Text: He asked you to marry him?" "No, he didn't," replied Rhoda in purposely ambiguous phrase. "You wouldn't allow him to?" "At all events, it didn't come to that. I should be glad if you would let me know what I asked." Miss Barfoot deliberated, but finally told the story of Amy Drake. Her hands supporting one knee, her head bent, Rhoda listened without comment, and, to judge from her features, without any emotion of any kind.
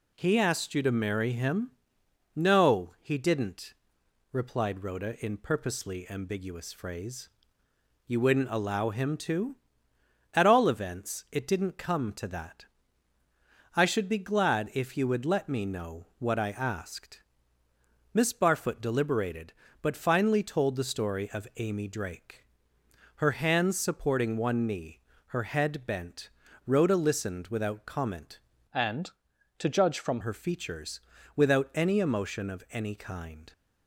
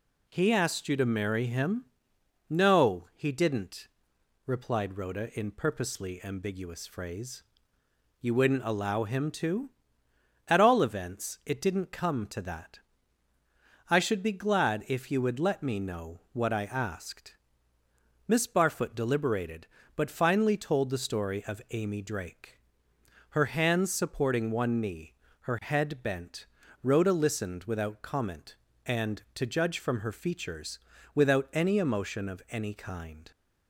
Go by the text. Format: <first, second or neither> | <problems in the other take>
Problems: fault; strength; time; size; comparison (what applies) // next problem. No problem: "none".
second | changes voice from "and" to "from"; from 28.7 to 30.2 s; 1.5 s long